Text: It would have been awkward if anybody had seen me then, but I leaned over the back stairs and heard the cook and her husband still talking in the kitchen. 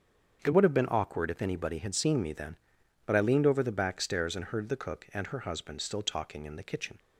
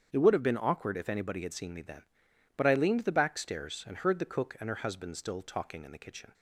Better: first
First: starts louder than the rest; strong; until 1.4 s; 7.5 dB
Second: starts louder than the rest; strong; until 1.1 s; 8 dB // skips "over"; at 3.0 s

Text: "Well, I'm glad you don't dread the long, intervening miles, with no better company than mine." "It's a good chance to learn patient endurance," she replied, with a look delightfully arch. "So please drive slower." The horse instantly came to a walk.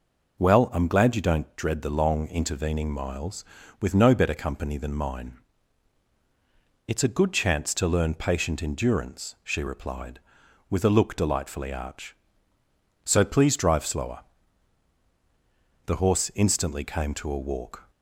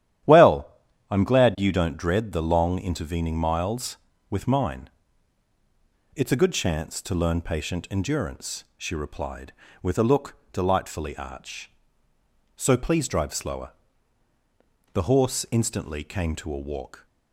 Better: first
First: none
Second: starts louder than the rest; strong; until 1.7 s; 11.5 dB // skips "no better company than"; at 4.4 s // pauses between "look" and "delightfully"; slight; at 10.3 s; 0.16 s long

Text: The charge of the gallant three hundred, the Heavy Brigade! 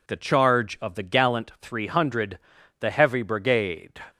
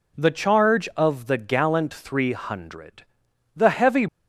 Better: first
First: none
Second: stops before "Brigade"; at 4.0 s

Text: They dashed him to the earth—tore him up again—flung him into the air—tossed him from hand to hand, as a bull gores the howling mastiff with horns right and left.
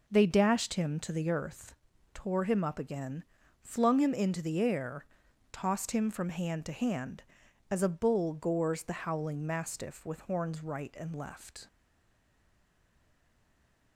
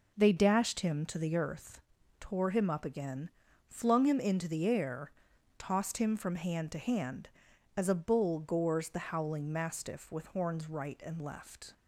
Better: second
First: stays silent after the last word; from 11.6 s on; 2.3 s long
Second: none

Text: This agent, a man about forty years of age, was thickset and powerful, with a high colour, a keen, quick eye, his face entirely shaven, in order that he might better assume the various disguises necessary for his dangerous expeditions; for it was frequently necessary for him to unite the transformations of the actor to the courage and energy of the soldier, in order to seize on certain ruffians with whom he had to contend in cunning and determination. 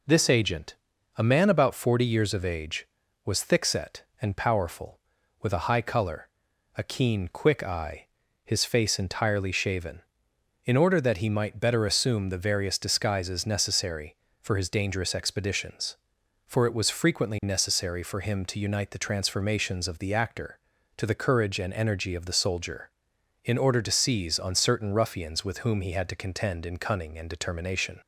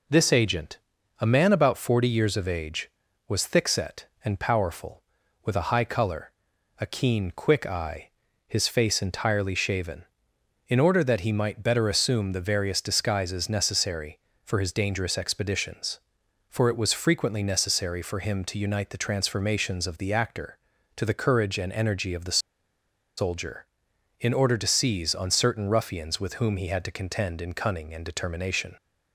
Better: first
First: none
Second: pauses between "the" and "soldier"; noticeable; at 22.3 s; 0.78 s long

